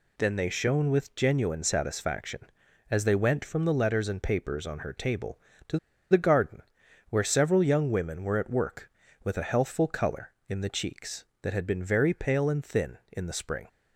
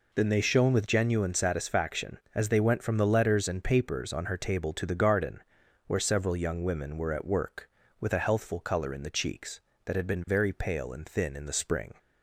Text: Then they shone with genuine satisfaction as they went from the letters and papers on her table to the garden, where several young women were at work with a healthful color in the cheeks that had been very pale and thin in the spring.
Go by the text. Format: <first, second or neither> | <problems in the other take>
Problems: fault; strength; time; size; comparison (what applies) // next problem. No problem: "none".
second | pauses between "to" and "the"; slight; at 5.7 s; 0.33 s long